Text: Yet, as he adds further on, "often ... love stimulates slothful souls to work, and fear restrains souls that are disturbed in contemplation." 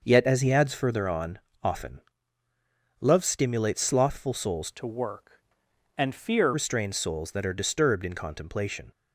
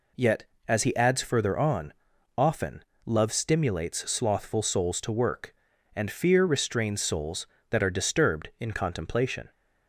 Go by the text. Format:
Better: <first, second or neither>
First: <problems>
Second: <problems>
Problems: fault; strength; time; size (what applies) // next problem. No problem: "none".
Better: second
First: changes voice from "to" to "fear"; from 4.7 to 6.5 s; 1.8 s long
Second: none